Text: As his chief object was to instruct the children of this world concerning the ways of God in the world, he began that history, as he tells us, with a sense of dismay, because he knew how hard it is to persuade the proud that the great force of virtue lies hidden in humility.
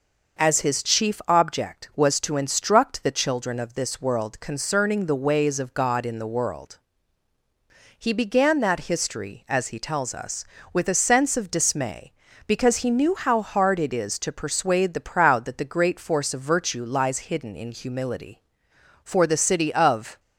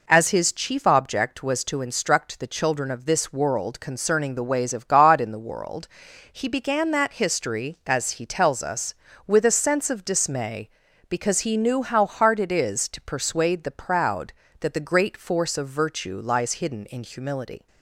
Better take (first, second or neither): second